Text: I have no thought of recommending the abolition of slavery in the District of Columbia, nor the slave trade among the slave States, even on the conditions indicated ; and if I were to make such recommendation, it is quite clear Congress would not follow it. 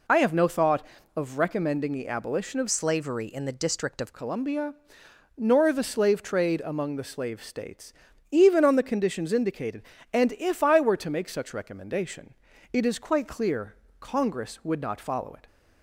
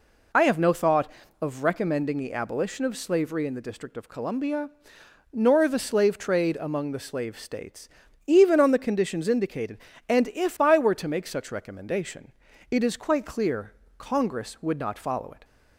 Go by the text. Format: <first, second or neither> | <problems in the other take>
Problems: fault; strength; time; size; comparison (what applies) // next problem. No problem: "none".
second | changes voice from "slavery" to "of"; from 2.7 to 4.1 s; 1.4 s long // pauses between "clear" and "Congress"; slight; at 13.7 s; 0.26 s long; slight in the second